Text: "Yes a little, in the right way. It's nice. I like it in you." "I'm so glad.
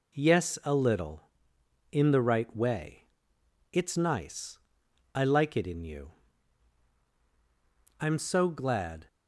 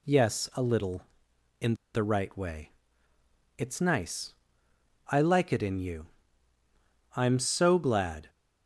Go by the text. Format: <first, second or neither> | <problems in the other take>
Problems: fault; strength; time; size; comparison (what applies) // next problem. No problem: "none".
first | pauses between "in" and "the"; slight; at 1.7 s; 0.18 s long